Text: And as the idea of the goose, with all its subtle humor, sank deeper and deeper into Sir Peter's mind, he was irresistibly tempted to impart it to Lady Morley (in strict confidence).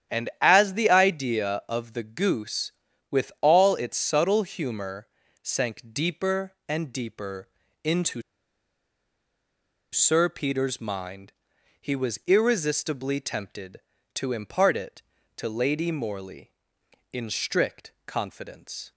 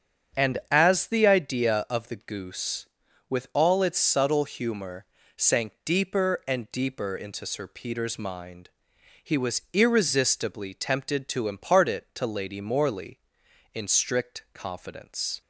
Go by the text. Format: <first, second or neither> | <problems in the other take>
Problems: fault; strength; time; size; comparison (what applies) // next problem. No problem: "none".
second | starts louder than the rest; strong; until 1.2 s; 9.5 dB; strong in the second // pauses between "deeper" and "into"; slight; at 7.4 s; 0.36 s long // pauses between "into" and "Sir"; strong; at 8.2 s; 1.7 s long